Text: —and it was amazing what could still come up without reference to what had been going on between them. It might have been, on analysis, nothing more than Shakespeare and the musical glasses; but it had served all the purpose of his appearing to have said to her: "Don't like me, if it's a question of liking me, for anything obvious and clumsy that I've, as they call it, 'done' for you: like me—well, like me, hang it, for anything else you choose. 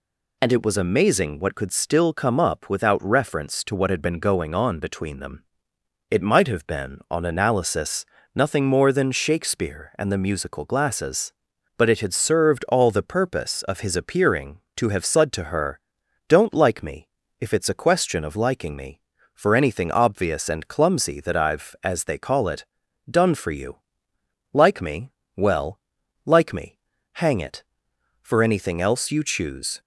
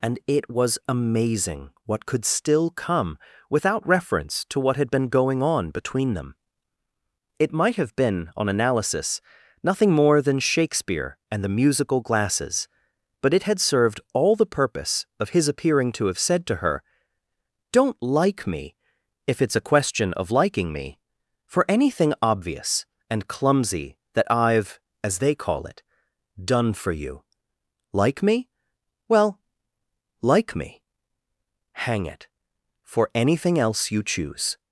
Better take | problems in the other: first | pauses between "amazing" and "what"; slight; at 1.7 s; 0.16 s long // skips "up"; at 3.3 s

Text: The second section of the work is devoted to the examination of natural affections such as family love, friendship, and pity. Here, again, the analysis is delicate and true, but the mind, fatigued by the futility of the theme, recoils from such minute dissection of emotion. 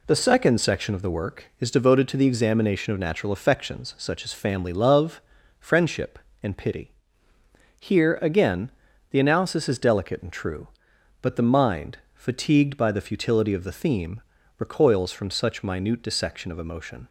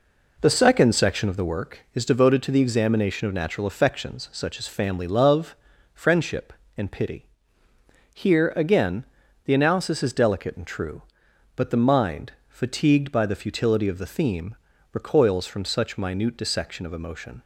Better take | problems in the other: first | starts louder than the rest; noticeable; until 1.5 s; 4 dB

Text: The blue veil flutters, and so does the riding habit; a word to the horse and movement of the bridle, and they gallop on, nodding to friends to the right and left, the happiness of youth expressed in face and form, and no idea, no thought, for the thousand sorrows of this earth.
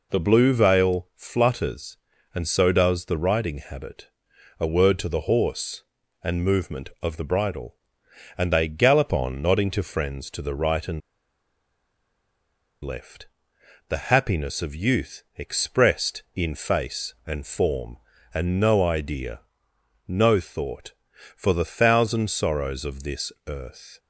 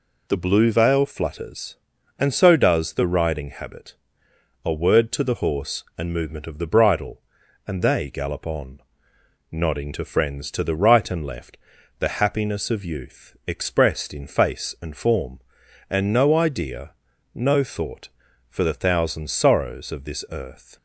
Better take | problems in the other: second | pauses between "and" and "left"; strong; at 11.0 s; 1.8 s long // pauses between "this" and "earth"; slight; at 23.3 s; 0.16 s long

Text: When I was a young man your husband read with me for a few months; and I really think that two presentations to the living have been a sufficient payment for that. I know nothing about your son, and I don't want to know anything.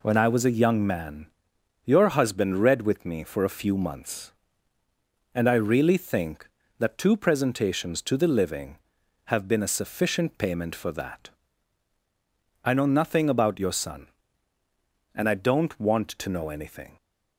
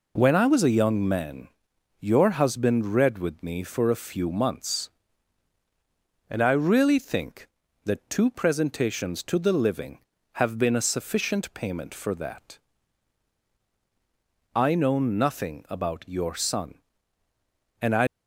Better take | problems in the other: first | pauses between "man" and "your"; noticeable; at 1.4 s; 0.52 s long; noticeable in the first // stops before "don't want to know anything"; at 18.0 s

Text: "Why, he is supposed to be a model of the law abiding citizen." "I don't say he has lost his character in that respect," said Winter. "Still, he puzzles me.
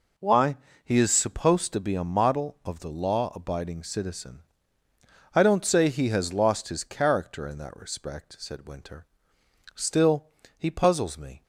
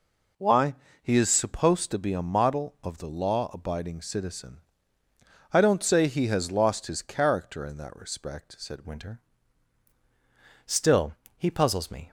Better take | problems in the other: first | changes voice at "Winter"; from 8.8 s on; 3.3 s long

